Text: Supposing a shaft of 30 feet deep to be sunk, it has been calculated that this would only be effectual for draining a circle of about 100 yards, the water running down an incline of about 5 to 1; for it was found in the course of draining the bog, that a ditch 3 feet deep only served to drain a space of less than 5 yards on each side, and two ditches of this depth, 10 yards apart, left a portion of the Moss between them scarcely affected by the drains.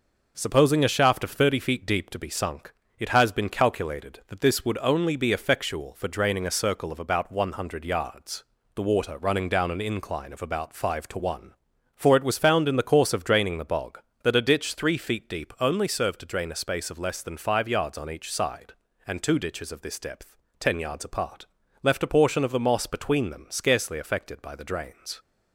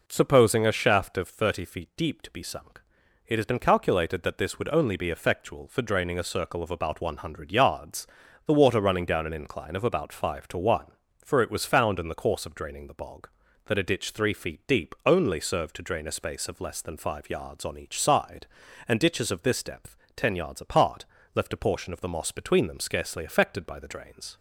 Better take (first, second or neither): first